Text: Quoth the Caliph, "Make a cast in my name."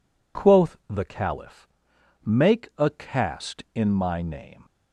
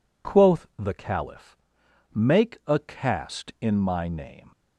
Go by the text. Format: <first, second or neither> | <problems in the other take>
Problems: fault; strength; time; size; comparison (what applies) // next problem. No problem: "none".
neither | none